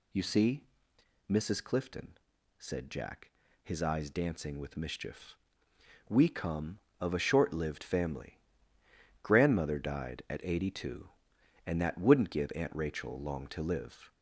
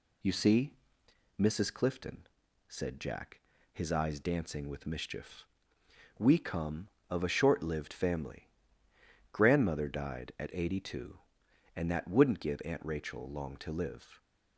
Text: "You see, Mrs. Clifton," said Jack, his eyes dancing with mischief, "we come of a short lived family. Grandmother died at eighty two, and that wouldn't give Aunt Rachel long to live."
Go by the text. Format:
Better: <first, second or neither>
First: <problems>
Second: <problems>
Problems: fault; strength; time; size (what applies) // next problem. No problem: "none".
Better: second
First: gets louder; slight; throughout; 3 dB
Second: none